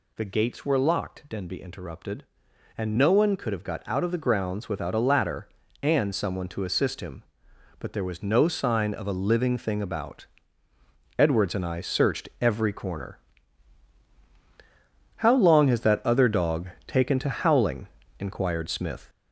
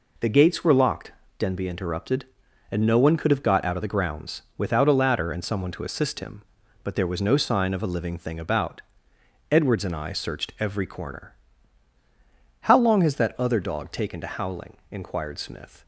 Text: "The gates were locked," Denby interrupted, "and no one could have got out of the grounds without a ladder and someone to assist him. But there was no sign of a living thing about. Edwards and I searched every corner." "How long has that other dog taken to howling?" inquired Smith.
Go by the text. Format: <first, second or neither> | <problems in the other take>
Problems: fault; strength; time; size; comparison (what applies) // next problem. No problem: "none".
second | gets louder; noticeable; throughout; 5 dB // pauses between "dog" and "taken"; slight; at 16.6 s; 0.20 s long